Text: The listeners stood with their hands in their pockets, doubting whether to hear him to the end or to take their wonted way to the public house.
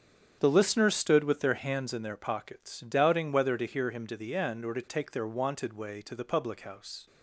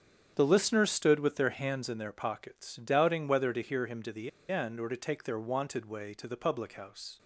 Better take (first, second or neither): first